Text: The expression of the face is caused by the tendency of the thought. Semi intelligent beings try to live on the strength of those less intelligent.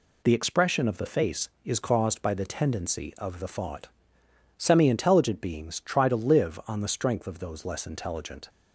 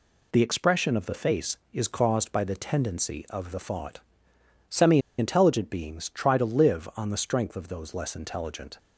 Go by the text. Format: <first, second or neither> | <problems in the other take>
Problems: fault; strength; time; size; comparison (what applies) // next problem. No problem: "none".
first | pauses between "Semi" and "intelligent"; slight; at 4.9 s; 0.19 s long